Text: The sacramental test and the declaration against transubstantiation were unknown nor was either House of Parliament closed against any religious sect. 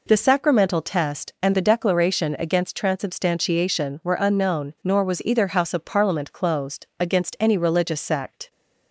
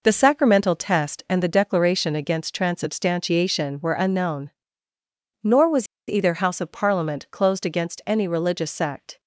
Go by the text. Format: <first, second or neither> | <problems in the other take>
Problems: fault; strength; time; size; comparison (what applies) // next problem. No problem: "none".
first | pauses between "unknown" and "nor"; noticeable; at 4.5 s; 0.90 s long // pauses between "was" and "either"; slight; at 5.8 s; 0.21 s long